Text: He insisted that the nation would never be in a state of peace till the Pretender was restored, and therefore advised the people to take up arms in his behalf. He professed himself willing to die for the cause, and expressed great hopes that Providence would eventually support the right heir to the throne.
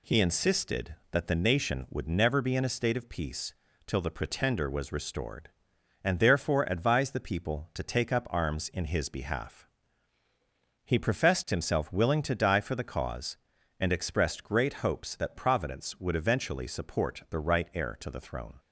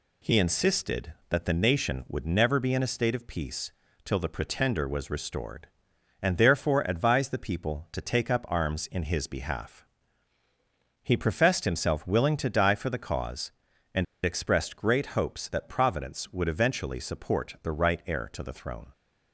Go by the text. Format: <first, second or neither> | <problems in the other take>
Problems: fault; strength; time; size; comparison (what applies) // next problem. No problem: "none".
first | pauses between "peace" and "till"; slight; at 3.7 s; 0.32 s long; slight in the first // pauses between "and" and "expressed"; slight; at 14.0 s; 0.20 s long